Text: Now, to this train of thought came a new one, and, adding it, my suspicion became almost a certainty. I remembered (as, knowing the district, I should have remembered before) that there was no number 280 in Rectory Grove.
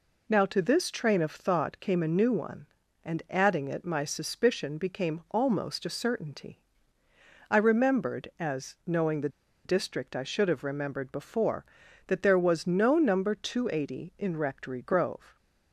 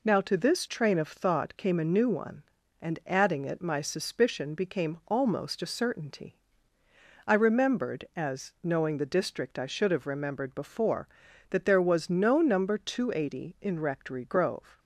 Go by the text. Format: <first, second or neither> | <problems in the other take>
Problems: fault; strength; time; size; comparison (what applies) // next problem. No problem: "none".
second | pauses between "the" and "district"; at 9.2 s; 0.36 s long